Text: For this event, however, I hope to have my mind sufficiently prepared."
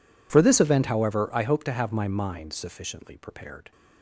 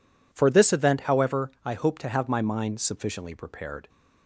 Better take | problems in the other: neither | none

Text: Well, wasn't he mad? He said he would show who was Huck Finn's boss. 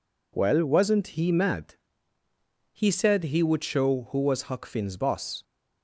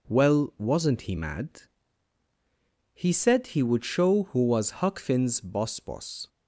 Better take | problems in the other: first | says "boss" twice; at 5.7 s

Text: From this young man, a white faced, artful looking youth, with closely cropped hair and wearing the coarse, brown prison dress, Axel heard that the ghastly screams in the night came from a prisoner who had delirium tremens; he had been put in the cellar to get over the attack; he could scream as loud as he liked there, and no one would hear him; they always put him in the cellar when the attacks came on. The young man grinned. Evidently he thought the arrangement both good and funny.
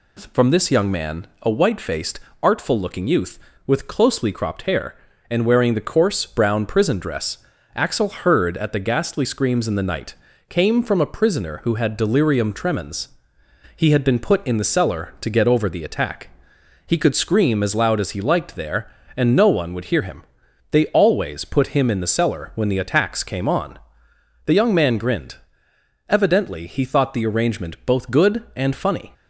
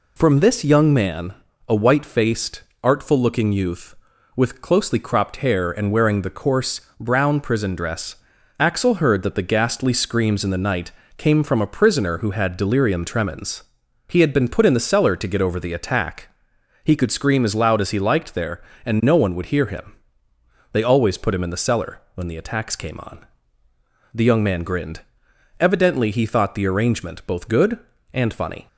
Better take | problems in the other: second | says "at" for "that"; at 8.5 s // pauses between "night" and "came"; slight; at 10.1 s; 0.34 s long; slight in the second

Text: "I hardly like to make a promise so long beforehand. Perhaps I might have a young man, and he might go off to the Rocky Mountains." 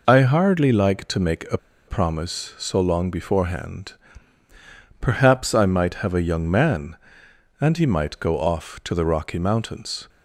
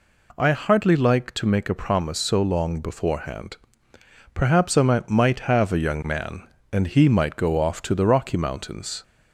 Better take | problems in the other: second | pauses between "a" and "promise"; slight; at 1.5 s; 0.30 s long

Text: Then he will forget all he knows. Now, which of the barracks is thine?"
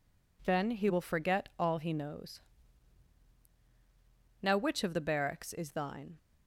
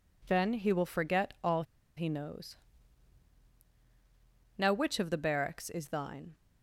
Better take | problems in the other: first | pauses between "all" and "he"; slight; at 1.6 s; 0.33 s long

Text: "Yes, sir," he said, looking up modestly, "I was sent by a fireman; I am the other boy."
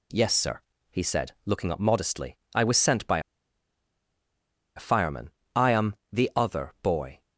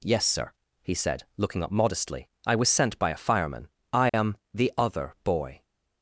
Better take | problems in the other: second | pauses between "by" and "a"; strong; at 3.1 s; 1.5 s long // pauses between "am" and "the"; slight; at 5.9 s; 0.18 s long; slight in the second

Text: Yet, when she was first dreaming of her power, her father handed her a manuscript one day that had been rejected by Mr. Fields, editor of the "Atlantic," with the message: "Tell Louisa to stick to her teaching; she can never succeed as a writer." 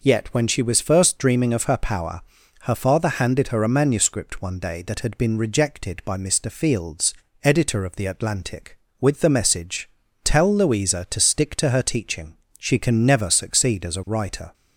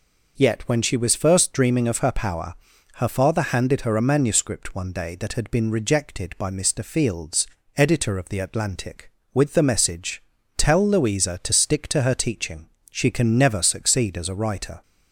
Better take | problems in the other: neither | none

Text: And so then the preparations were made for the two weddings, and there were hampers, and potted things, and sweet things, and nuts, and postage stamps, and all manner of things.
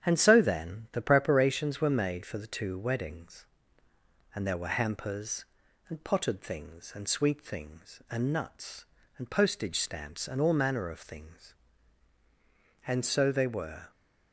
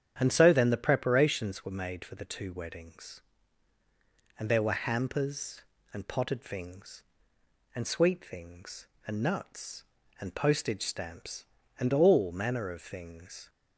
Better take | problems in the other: second | starts louder than the rest; strong; until 1.1 s; 9 dB; strong in the second // goes on to say "And so they were"; noticeable; from 12.8 s on; 1.0 s long

